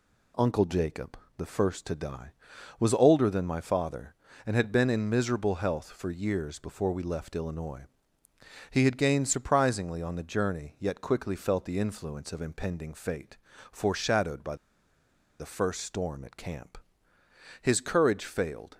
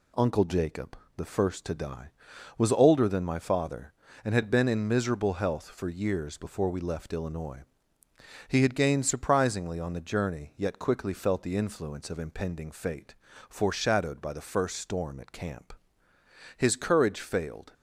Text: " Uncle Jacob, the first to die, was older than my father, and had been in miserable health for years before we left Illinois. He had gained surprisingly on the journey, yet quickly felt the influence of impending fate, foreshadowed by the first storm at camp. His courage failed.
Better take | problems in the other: second | pauses between "by" and "the"; noticeable; at 14.5 s; 0.84 s long

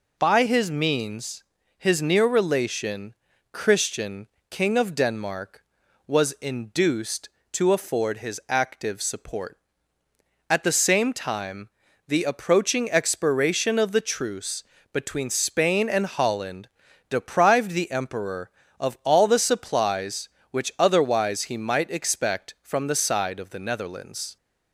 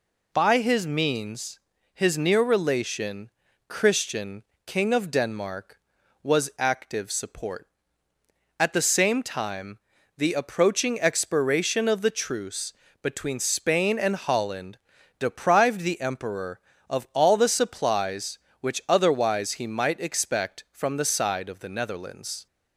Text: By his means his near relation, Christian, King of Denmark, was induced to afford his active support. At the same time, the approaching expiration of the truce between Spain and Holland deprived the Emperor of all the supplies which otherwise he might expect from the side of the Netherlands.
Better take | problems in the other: first | pauses between "means" and "his"; slight; at 1.5 s; 0.36 s long; slight in the first // skips "induced to afford his"; at 6.5 s // pauses between "truce" and "between"; slight; at 12.7 s; 0.28 s long; slight in the first // pauses between "Holland" and "deprived"; at 14.7 s; 0.42 s long; also in the first

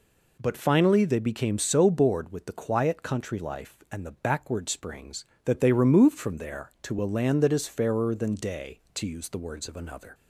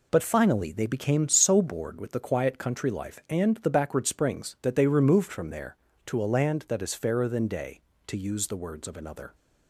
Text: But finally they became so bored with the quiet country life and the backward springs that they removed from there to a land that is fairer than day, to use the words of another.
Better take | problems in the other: neither | none

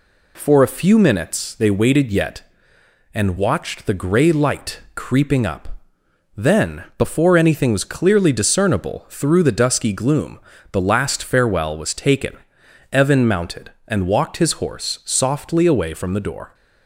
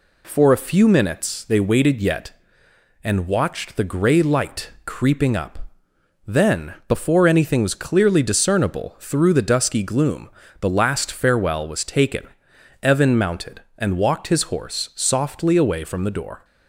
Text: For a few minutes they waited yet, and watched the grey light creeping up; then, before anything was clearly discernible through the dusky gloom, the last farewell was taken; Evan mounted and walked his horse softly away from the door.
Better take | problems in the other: neither | none

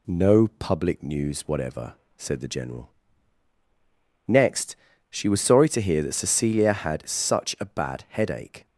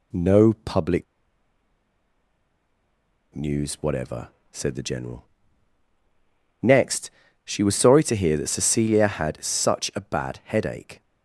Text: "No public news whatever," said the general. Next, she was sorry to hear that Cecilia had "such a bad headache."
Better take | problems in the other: first | pauses between "public" and "news"; strong; at 1.0 s; 2.3 s long

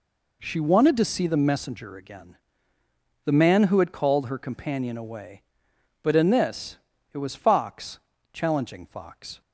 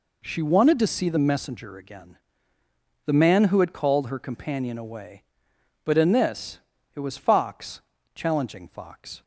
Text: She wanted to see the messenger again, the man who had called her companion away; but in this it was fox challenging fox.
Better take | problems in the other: neither | pauses between "this" and "it"; slight; the same in both // pauses between "fox" and "challenging"; slight; the same in both

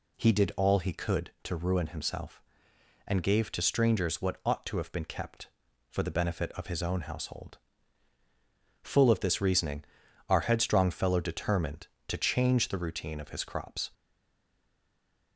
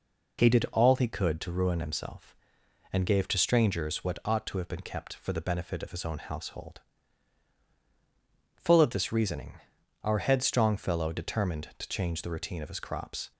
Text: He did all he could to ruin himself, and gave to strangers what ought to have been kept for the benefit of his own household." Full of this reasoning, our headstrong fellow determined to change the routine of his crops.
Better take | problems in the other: second | stays silent after the last word; noticeable; from 13.9 s on; 1.4 s long

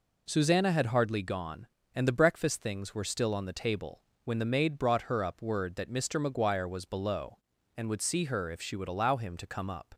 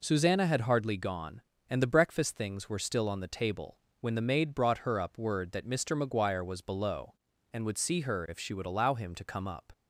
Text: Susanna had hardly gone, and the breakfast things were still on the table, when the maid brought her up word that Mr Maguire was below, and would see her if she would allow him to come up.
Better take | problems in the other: neither | none

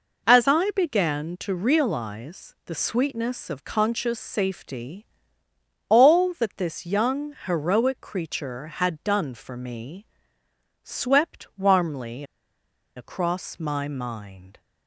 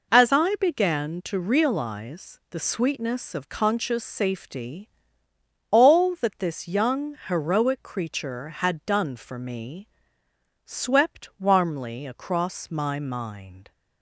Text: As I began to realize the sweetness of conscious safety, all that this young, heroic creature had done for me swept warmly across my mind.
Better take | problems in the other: second | pauses between "me" and "swept"; noticeable; at 10.0 s; 0.76 s long; noticeable in the second // pauses between "warmly" and "across"; noticeable; at 12.2 s; 0.73 s long

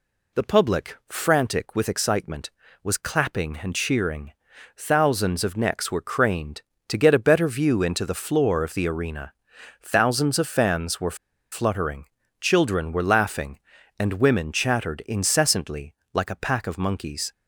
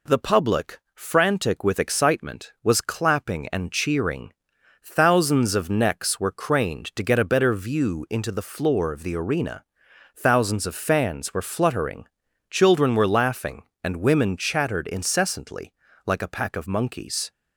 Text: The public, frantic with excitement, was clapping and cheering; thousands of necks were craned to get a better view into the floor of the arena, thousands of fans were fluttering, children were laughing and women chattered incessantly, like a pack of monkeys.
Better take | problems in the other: second | pauses between "were" and "fluttering"; slight; at 11.1 s; 0.35 s long

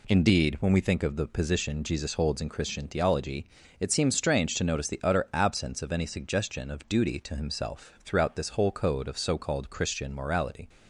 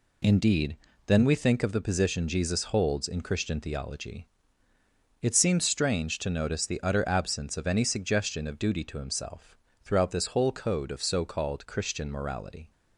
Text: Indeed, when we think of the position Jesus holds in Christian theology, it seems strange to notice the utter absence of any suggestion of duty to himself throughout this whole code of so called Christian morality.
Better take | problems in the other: first | says "then" for "when"; at 1.0 s // pauses between "himself" and "throughout"; slight; at 9.5 s; 0.30 s long

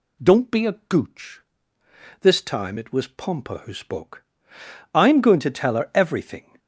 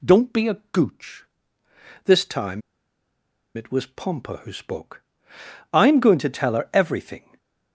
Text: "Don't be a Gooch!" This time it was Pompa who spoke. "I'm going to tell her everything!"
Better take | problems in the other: first | pauses between "time" and "it"; noticeable; at 2.6 s; 0.94 s long // stays silent after the last word; slight; from 7.1 s on; 0.6 s long

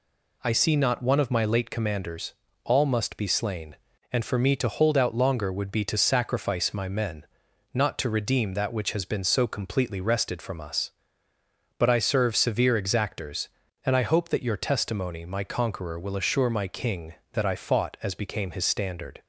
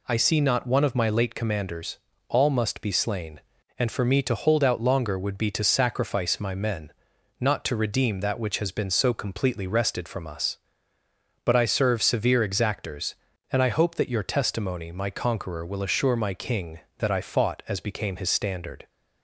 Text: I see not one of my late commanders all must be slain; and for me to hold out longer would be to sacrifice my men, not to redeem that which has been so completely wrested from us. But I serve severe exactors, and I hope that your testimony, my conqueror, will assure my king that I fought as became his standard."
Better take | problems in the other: neither | pauses between "commanders" and "all"; slight; the same in both

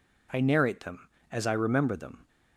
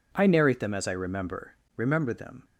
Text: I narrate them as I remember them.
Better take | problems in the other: first | says "remember" twice; at 1.7 s

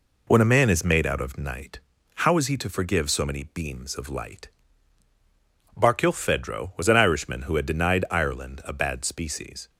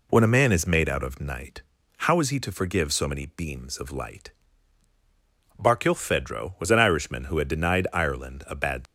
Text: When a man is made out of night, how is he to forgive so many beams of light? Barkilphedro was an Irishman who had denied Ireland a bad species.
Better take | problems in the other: first | stops before "species"; at 8.8 s

